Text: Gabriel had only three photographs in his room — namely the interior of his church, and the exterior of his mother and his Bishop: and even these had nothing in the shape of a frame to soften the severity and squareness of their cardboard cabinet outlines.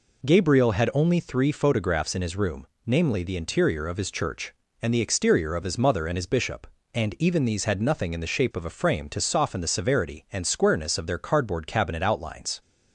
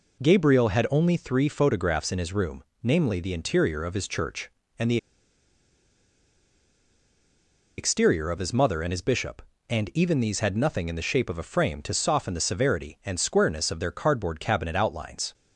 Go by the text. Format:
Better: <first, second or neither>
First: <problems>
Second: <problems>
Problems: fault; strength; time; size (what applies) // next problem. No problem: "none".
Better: first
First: none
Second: pauses between "the" and "exterior"; strong; at 4.9 s; 2.8 s long